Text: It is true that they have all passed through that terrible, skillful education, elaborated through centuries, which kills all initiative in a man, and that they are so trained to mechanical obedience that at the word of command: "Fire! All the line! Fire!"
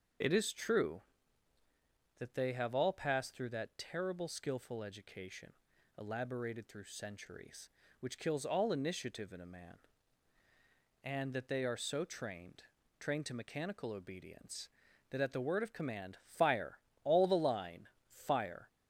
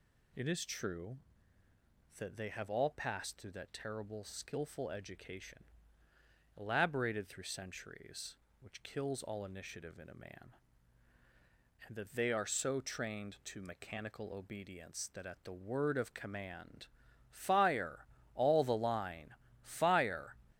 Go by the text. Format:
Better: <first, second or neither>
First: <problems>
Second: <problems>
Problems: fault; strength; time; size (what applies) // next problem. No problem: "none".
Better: second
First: says "trained" twice; at 12.9 s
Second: none